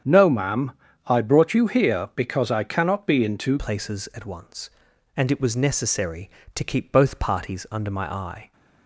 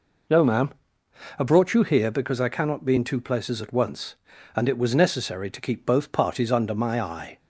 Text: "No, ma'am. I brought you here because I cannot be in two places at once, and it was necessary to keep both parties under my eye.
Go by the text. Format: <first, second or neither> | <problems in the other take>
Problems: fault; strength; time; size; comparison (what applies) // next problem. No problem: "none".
second | starts louder than the rest; strong; until 1.4 s; 8.5 dB // changes voice at "places"; from 3.5 s on; 5.0 s long